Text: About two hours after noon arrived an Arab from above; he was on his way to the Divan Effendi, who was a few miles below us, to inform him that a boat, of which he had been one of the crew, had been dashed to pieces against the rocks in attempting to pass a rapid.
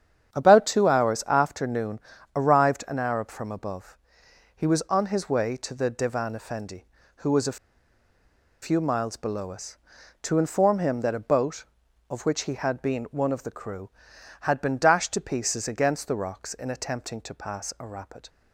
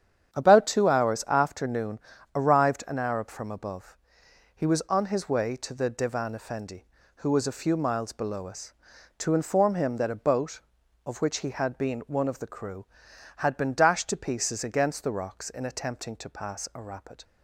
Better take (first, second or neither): second